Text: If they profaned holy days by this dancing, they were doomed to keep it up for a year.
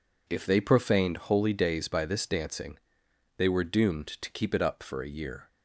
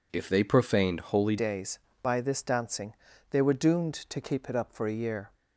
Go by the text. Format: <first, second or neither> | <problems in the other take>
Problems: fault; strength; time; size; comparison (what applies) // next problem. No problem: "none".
first | changes voice at "days"; from 1.3 s on; 4.0 s long